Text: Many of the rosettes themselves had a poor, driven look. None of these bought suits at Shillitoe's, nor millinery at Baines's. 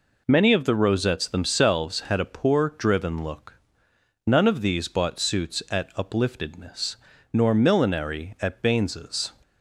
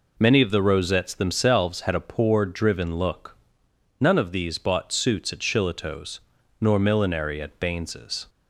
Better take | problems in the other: second | says "Upliftedness" for "Shillitoe's"; at 5.9 s

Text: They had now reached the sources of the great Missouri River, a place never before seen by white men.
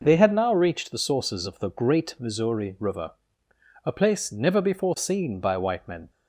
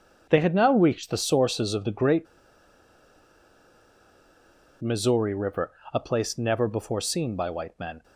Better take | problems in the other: first | pauses between "great" and "Missouri"; strong; at 2.2 s; 2.5 s long

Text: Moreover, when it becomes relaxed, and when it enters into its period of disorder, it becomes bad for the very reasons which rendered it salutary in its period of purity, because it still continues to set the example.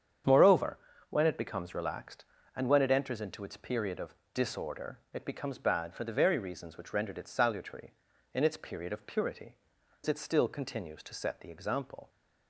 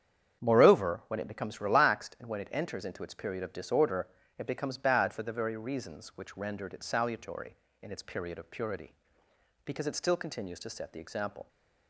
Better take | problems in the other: second | starts louder than the rest; strong; until 1.5 s; 8 dB; strong in the second // pauses between "of" and "disorder"; slight; at 4.1 s; 0.18 s long // skips "because"; at 9.7 s

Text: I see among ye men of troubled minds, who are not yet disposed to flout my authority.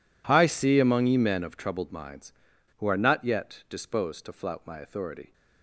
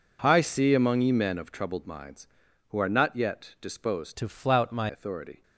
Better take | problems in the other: first | changes voice from "to" to "my"; from 4.1 to 4.8 s; 0.7 s long

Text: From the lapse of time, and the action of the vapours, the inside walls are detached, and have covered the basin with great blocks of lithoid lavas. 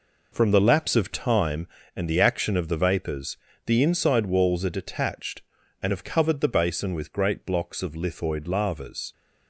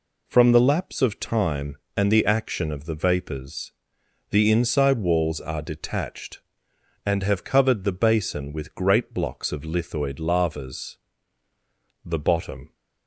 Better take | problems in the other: first | goes on to say "The bottom"; noticeable; from 12.0 s on; 0.70 s long

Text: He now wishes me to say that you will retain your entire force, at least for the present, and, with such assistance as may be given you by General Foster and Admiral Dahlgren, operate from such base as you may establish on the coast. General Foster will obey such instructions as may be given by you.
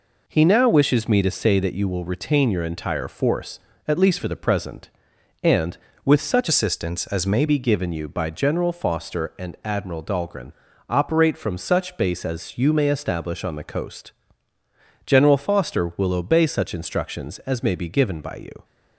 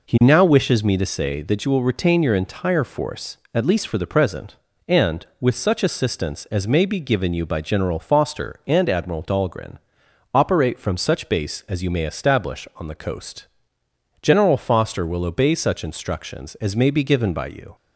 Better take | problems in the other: second | changes voice from "assistance" to "may"; from 6.4 to 7.4 s; 1.0 s long

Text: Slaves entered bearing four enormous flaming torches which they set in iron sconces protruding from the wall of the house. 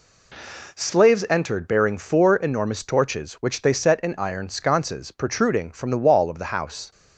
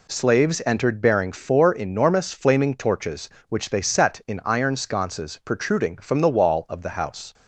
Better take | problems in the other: second | skips "flaming"; at 2.8 s

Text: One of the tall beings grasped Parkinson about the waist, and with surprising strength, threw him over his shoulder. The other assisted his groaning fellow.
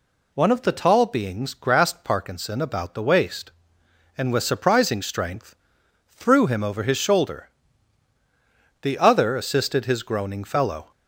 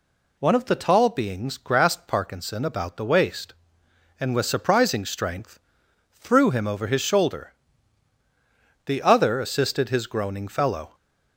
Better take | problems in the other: neither | none

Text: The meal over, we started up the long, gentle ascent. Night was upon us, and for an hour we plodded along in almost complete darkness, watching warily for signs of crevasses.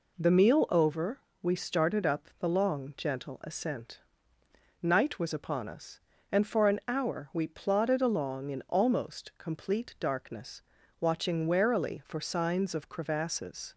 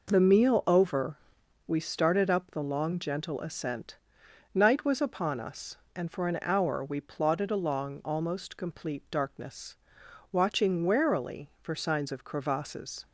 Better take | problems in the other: first | skips "in"; at 8.0 s

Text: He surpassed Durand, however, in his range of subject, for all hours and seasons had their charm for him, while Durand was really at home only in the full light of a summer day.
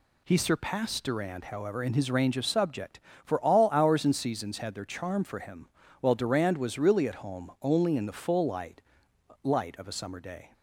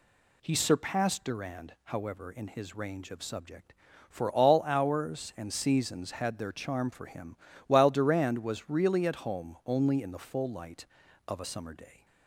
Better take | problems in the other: second | says "light" twice; at 9.4 s

